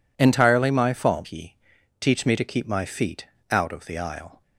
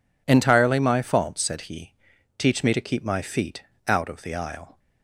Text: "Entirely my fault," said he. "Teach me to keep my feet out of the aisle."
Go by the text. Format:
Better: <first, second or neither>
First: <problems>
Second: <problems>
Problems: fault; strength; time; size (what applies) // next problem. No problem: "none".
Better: second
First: skips "said"; at 1.2 s // pauses between "feet" and "out"; slight; at 3.2 s; 0.24 s long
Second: pauses between "feet" and "out"; slight; at 3.6 s; 0.24 s long